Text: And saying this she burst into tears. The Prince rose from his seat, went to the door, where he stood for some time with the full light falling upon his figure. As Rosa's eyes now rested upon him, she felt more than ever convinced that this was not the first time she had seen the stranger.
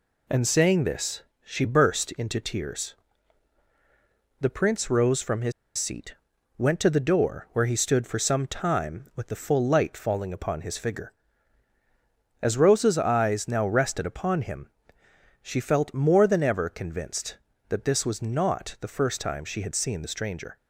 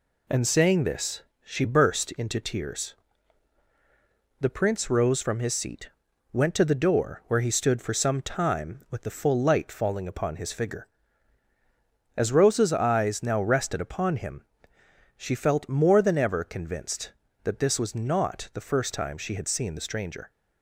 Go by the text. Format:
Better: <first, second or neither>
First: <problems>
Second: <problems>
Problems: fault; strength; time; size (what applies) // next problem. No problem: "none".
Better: second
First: pauses between "this" and "she"; slight; at 1.2 s; 0.22 s long // pauses between "his" and "seat"; slight; at 5.5 s; 0.26 s long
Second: pauses between "this" and "she"; slight; at 1.2 s; 0.22 s long